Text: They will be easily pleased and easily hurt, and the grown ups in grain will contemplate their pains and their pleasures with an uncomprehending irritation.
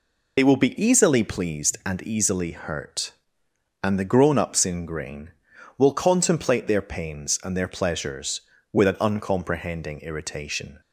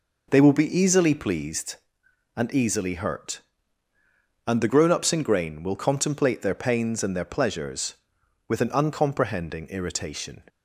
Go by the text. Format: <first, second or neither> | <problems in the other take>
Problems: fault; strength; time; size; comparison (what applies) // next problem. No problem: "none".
second | loses the start of "They"; at 0.3 s; 50 ms